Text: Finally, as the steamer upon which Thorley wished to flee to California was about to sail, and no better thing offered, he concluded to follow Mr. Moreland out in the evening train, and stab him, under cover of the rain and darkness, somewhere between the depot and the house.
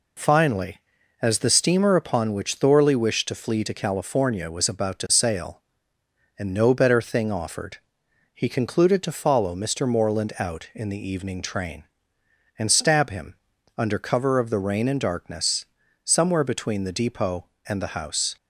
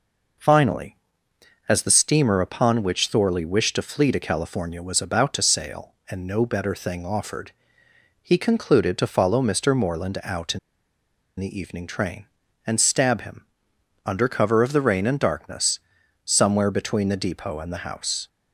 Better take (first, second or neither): first